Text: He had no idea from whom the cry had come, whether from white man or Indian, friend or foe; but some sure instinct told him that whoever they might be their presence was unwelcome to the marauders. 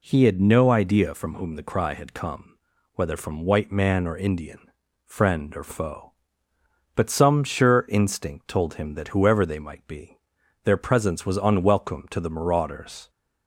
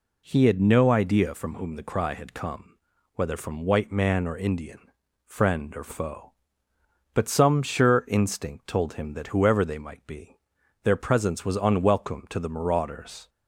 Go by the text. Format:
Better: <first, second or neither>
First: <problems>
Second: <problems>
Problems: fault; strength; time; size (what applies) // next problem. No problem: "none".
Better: neither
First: pauses between "be" and "their"; noticeable; at 10.1 s; 0.46 s long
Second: pauses between "be" and "their"; noticeable; at 10.3 s; 0.46 s long